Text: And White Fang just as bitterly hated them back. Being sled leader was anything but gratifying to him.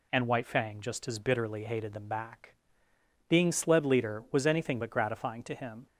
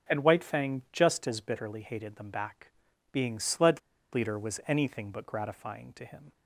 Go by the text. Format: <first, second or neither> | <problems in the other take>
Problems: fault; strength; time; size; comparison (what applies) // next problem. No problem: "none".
first | pauses between "sled" and "leader"; slight; at 3.7 s; 0.33 s long